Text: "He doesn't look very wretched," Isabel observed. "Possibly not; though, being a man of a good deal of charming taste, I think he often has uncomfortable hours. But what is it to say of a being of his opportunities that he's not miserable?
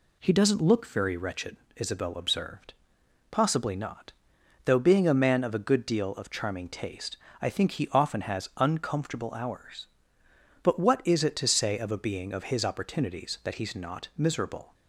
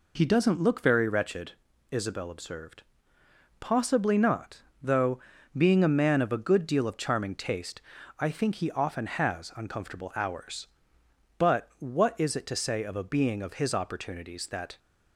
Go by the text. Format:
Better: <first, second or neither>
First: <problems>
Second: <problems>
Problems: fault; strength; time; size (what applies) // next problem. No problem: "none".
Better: first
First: none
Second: stops before "he's not miserable"; at 14.7 s